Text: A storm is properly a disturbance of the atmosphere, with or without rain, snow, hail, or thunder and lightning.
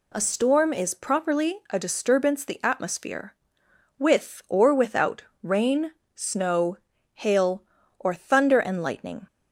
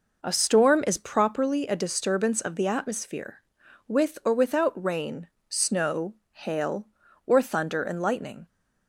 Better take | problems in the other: second | skips "of"; at 2.4 s // pauses between "without" and "rain"; slight; at 5.2 s; 0.20 s long

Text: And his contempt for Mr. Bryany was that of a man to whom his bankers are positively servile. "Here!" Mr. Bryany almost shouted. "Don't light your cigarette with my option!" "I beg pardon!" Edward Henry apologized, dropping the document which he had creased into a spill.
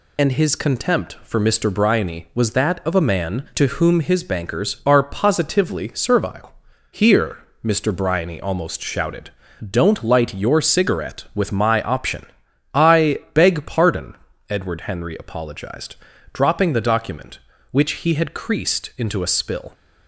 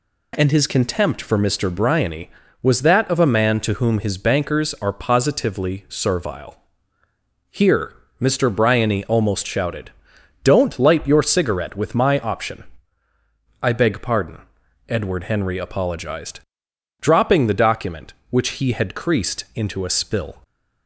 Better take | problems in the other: second | loses the start of "And"; at 0.1 s; 30 ms // pauses between "I" and "beg"; slight; at 13.1 s; 0.16 s long

